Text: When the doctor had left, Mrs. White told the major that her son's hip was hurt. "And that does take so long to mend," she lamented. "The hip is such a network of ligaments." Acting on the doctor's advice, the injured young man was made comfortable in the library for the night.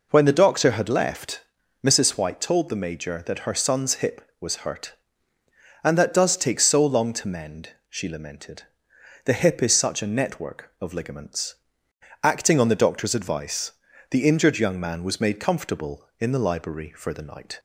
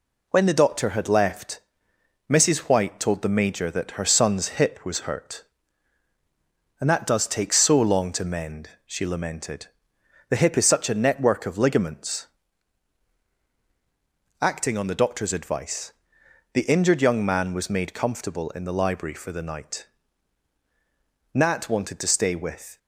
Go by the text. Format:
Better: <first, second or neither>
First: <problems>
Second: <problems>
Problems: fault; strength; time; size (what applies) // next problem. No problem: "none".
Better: first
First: none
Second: goes on to say "Nat wanted to stay with"; from 21.3 s on; 1.4 s long